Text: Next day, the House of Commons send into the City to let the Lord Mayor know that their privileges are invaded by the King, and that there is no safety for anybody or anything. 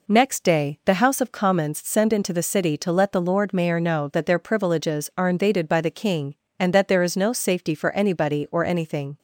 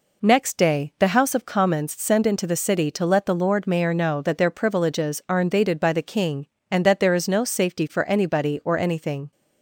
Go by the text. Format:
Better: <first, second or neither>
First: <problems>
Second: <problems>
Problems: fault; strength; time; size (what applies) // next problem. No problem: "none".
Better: neither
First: none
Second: none